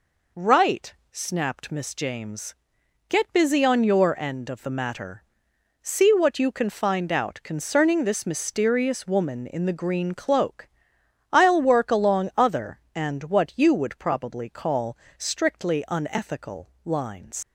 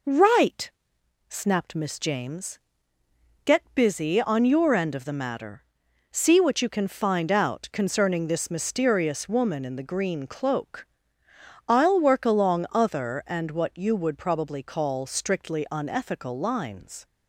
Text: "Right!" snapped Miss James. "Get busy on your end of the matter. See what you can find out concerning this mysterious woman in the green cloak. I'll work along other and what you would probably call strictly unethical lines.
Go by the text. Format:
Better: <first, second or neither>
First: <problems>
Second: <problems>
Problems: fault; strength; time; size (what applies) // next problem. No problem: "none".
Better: second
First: pauses between "call" and "strictly"; slight; at 14.9 s; 0.22 s long // leaves "lines" unfinished; at 17.4 s; 70 ms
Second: none